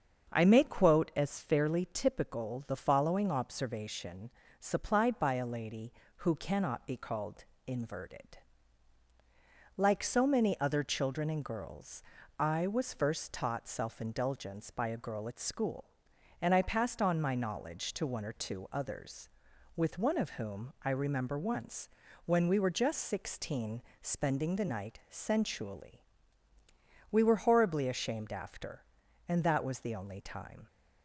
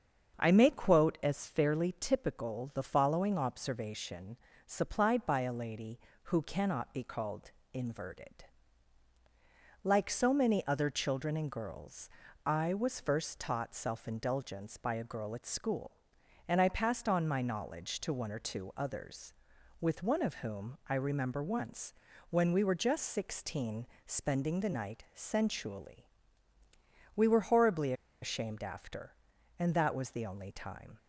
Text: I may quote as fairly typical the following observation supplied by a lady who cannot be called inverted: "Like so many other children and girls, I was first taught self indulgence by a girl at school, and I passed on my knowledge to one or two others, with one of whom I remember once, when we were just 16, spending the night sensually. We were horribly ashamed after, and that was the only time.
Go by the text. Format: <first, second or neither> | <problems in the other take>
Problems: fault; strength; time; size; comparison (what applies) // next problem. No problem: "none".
first | starts louder than the rest; until 1.4 s; 7 dB; also in the first // pauses between "observation" and "supplied"; slight; at 4.3 s; 0.30 s long; slight in the first // pauses between "called" and "inverted"; slight; at 7.5 s; 0.22 s long; slight in the first // pauses between "horribly" and "ashamed"; slight; at 27.9 s; 0.29 s long